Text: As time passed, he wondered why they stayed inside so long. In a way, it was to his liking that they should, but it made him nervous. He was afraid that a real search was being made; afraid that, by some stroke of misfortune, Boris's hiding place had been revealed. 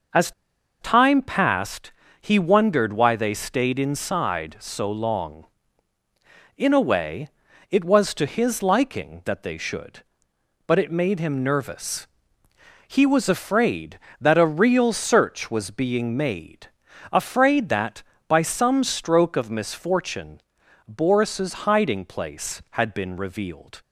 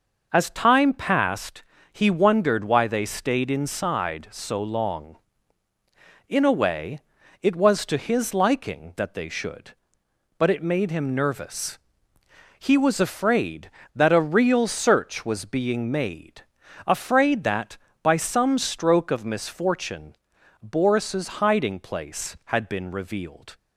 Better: second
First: pauses between "As" and "time"; noticeable; at 0.3 s; 0.50 s long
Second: none

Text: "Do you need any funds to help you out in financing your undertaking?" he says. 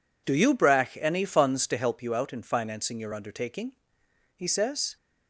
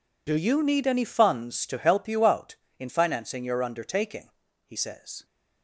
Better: second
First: says "brach" for "need"; at 0.5 s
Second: none

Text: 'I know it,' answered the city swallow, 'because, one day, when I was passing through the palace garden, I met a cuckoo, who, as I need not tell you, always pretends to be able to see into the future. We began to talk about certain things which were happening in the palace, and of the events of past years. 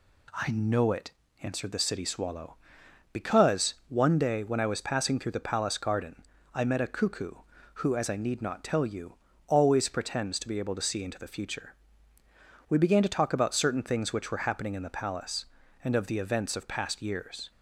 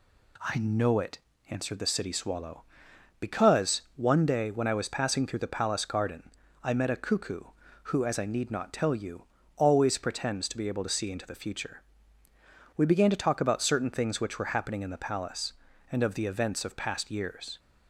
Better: neither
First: none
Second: none

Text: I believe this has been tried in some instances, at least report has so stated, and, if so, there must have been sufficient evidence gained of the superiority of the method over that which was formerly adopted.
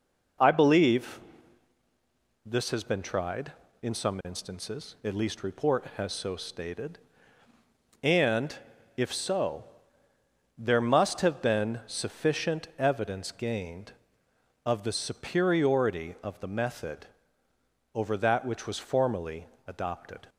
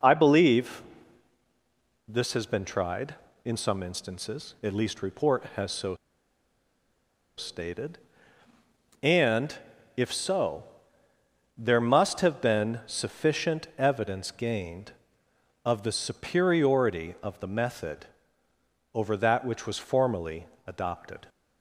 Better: first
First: pauses between "believe" and "this"; strong; at 1.1 s; 1.2 s long // pauses between "method" and "over"; noticeable; at 17.0 s; 0.88 s long // pauses between "formerly" and "adopted"; slight; at 19.4 s; 0.20 s long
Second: pauses between "believe" and "this"; strong; at 0.8 s; 1.2 s long // pauses between "so" and "stated"; strong; at 5.9 s; 1.4 s long // pauses between "method" and "over"; noticeable; at 18.0 s; 0.88 s long // pauses between "formerly" and "adopted"; slight; at 20.4 s; 0.20 s long

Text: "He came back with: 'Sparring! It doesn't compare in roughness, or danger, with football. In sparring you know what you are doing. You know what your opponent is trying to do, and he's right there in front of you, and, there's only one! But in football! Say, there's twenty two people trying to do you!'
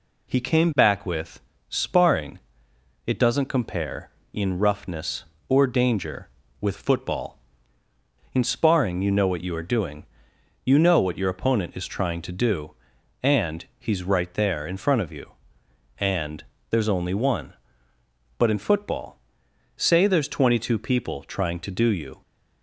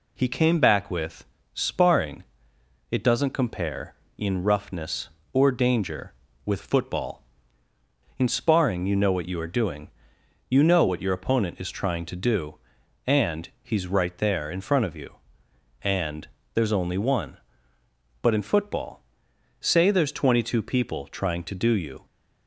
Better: neither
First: none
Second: none

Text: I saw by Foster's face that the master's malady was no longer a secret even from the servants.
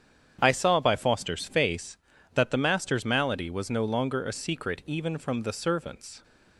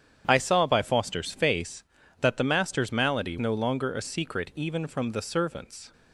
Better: first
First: starts louder than the rest; strong; until 1.4 s; 8.5 dB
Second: starts louder than the rest; strong; until 1.2 s; 9 dB // skips "was"; at 3.3 s

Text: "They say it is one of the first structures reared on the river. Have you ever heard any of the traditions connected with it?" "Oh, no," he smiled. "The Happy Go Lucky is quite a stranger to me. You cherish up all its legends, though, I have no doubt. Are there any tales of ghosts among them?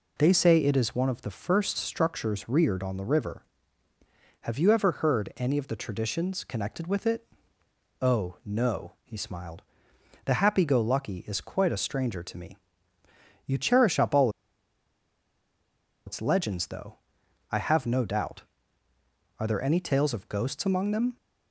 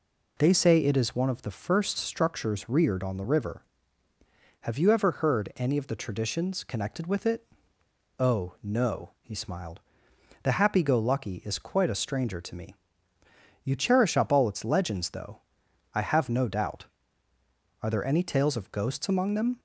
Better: second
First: pauses between "all" and "its"; strong; at 14.2 s; 1.7 s long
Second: none

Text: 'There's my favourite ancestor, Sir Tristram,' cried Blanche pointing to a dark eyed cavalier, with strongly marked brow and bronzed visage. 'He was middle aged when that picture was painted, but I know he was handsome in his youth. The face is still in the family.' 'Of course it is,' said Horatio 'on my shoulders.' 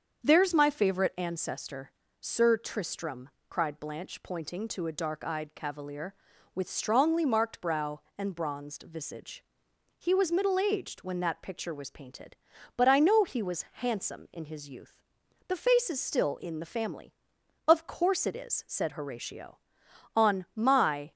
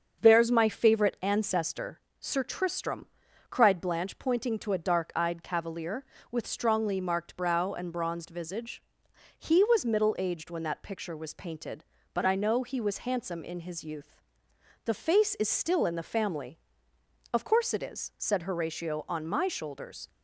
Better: second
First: starts louder than the rest; until 1.2 s; 7 dB // stops before "shoulders"; at 21.1 s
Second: starts louder than the rest; until 1.2 s; 6.5 dB

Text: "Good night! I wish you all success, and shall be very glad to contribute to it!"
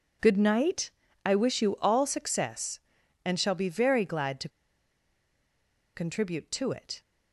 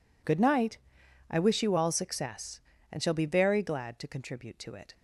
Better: second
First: pauses between "to" and "contribute"; strong; at 4.4 s; 1.4 s long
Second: none

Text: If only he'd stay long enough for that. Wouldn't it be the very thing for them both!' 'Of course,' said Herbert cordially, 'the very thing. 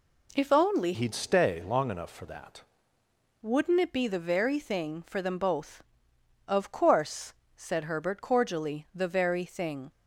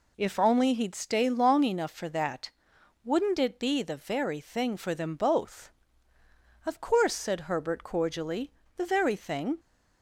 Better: second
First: changes voice from "he'd" to "that"; from 0.9 to 2.6 s; 1.7 s long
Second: none

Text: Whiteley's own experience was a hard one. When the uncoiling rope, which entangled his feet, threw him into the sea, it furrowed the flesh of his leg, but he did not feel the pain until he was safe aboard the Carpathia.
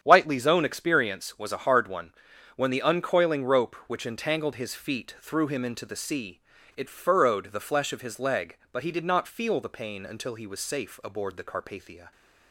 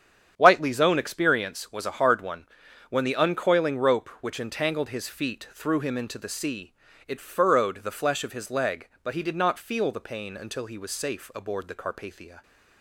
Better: neither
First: starts louder than the rest; strong; until 1.0 s; 8.5 dB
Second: starts louder than the rest; strong; until 1.3 s; 8 dB

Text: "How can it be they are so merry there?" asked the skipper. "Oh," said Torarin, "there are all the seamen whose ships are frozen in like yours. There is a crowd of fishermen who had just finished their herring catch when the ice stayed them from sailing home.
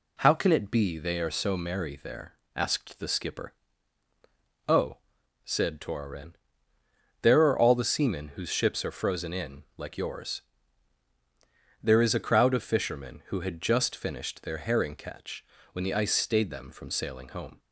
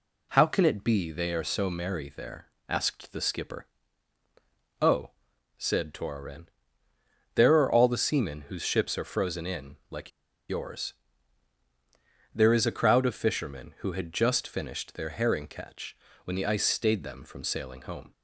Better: first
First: pauses between "catch" and "when"; slight; at 15.4 s; 0.30 s long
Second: pauses between "like" and "yours"; at 10.1 s; 0.39 s long // pauses between "catch" and "when"; slight; at 15.9 s; 0.30 s long

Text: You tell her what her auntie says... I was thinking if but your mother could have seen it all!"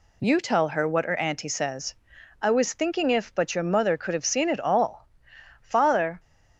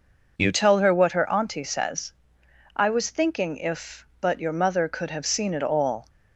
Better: second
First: goes on to say "Father"; from 5.6 s on; 0.58 s long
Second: none

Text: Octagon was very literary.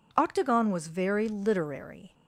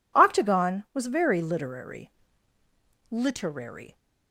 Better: first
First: none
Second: says "literary" twice; at 3.0 s

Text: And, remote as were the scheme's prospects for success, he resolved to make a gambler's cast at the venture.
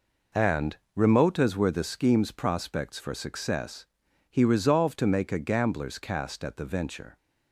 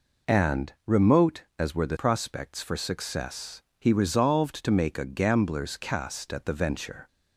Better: first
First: none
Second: skips "scheme's"; at 1.9 s

